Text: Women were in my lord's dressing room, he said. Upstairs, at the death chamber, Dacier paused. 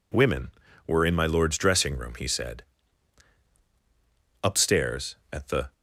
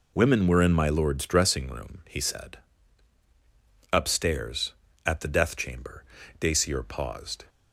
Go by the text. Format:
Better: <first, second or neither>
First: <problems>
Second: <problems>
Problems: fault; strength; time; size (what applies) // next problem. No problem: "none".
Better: second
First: stops before "death chamber Dacier paused"; at 5.7 s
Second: none